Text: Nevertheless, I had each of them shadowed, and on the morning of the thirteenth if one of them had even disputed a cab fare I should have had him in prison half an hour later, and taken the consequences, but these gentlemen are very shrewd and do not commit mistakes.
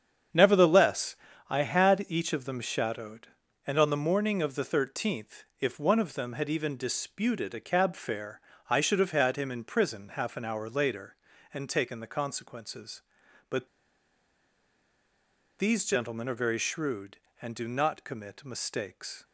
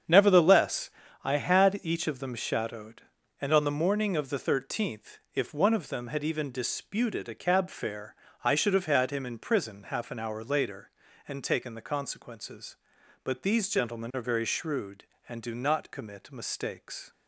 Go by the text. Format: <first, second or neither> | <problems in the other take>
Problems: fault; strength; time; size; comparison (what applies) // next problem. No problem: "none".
second | starts louder than the rest; strong; until 1.6 s; 8 dB; strong in the second // pauses between "thirteenth" and "if"; slight; at 5.4 s; 0.16 s long; slight in the second // pauses between "fare" and "I"; slight; at 8.3 s; 0.30 s long; slight in the second // pauses between "but" and "these"; strong; at 13.6 s; 1.9 s long